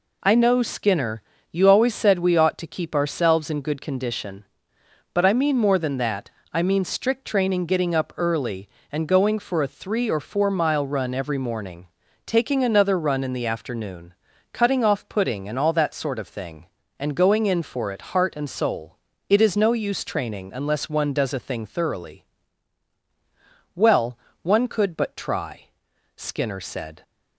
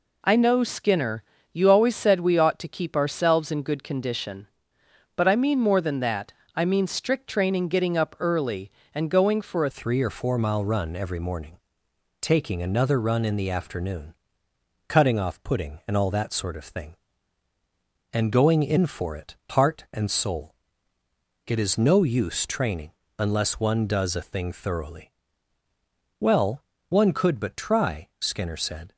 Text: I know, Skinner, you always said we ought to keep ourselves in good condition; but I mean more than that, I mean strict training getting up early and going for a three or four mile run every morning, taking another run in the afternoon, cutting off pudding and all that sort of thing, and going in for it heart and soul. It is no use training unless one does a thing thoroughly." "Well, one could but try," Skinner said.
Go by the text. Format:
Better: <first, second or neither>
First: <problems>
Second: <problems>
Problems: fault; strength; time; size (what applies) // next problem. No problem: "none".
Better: first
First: none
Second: changes voice at "three"; from 9.7 s on; 19.2 s long // pauses between "training" and "unless"; slight; at 22.9 s; 0.26 s long